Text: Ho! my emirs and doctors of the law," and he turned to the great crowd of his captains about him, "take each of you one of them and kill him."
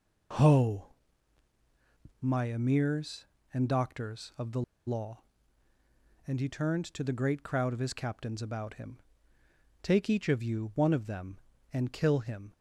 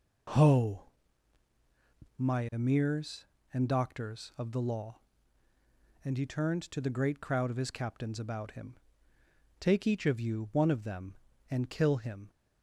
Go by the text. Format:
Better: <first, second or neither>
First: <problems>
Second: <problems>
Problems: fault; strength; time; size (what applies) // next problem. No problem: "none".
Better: second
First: pauses between "the" and "law"; slight; at 4.6 s; 0.25 s long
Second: none